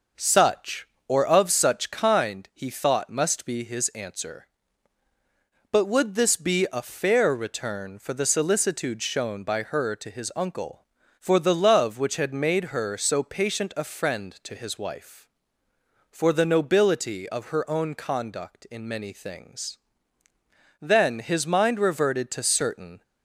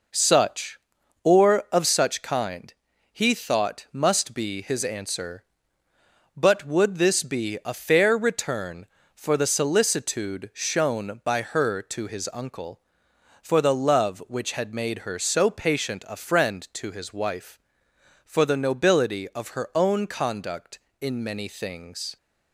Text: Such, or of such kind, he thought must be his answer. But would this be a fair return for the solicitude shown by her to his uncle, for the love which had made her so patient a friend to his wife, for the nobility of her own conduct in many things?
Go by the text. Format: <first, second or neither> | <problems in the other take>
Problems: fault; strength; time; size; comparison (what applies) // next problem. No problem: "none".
second | goes on to say "Then his mind reverted to certain"; strong; from 20.8 s on; 2.2 s long